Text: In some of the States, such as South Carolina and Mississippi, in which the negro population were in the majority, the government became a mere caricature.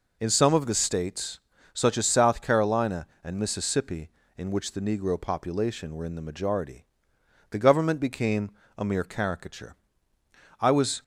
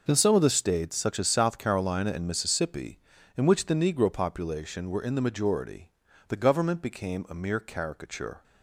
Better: second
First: pauses between "became" and "a"; slight; at 8.5 s; 0.28 s long // goes on to say "I was"; slight; from 10.6 s on; 0.42 s long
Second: none

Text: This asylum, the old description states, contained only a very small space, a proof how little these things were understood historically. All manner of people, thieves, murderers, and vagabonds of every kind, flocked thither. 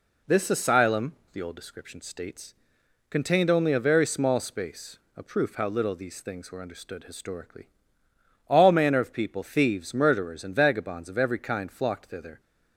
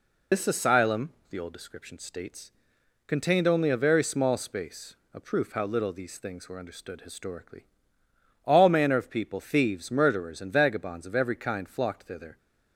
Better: first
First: none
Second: loses the start of "This"; at 0.3 s; 90 ms

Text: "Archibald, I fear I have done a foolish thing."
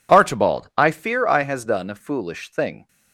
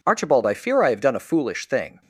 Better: second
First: says "has" for "have"; at 1.4 s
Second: none

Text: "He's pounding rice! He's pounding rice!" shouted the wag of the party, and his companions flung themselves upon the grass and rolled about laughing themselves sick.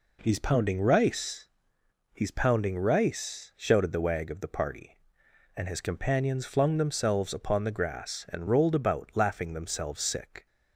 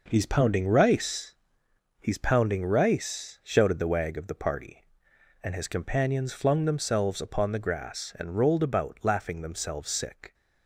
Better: first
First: none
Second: gets quieter; strong; throughout; 7.5 dB

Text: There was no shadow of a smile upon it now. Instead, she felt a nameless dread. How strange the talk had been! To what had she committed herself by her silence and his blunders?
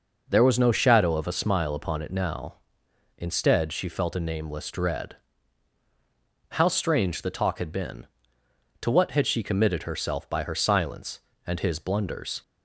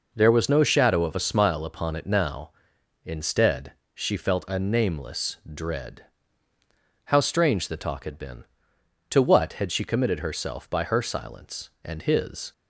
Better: first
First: none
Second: stops before "blunders"; at 12.5 s

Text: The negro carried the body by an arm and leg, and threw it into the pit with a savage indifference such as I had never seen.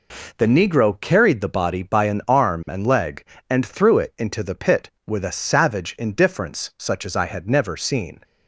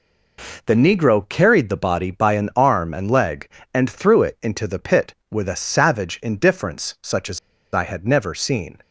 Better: first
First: none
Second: pauses between "as" and "I"; slight; at 7.3 s; 0.36 s long

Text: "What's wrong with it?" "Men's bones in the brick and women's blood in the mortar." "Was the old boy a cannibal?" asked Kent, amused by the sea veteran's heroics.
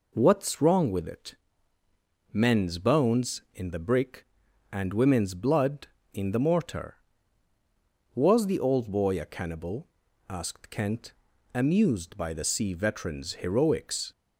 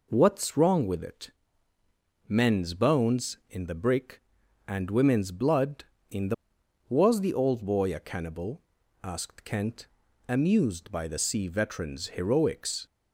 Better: first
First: none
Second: skips "mortar"; at 6.6 s

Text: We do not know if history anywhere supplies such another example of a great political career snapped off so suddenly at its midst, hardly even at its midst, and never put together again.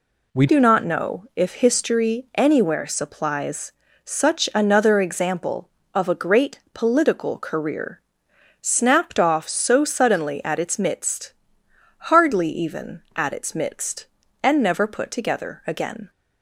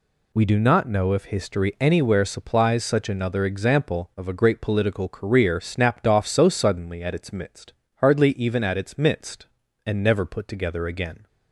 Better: second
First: changes voice at "do"; from 0.4 s on; 15.6 s long // pauses between "supplies" and "such"; slight; at 3.7 s; 0.32 s long // pauses between "career" and "snapped"; noticeable; at 7.9 s; 0.60 s long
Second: none

